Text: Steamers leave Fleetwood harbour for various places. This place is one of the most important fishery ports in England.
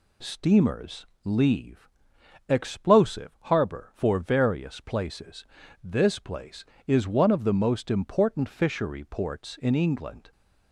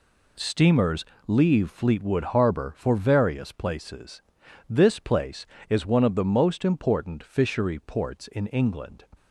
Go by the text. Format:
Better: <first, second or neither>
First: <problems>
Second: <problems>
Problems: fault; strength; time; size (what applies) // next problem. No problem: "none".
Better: second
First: pauses between "Steamers" and "leave"; slight; at 1.0 s; 0.18 s long // says "Explosive" for "Fleetwood"; at 2.4 s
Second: pauses between "Steamers" and "leave"; slight; at 1.0 s; 0.20 s long